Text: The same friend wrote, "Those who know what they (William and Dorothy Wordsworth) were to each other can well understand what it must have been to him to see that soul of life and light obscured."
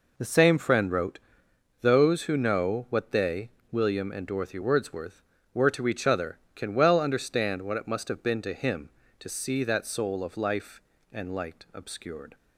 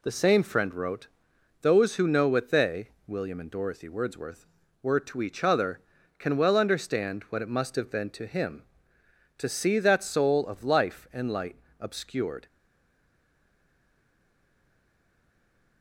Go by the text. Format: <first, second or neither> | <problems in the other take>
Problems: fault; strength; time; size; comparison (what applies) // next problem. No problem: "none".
first | pauses between "light" and "obscured"; slight; at 11.5 s; 0.24 s long // stays silent after the last word; strong; from 12.4 s on; 3.4 s long